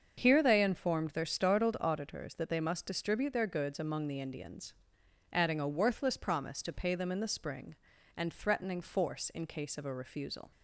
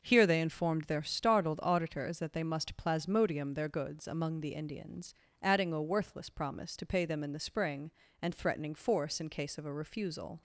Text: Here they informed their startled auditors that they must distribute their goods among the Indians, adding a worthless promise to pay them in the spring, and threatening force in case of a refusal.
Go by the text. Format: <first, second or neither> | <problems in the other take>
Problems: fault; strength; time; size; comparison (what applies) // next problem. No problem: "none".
first | starts louder than the rest; noticeable; until 1.0 s; 6 dB; also in the first // says "plasmodium" for "distribute"; at 2.7 s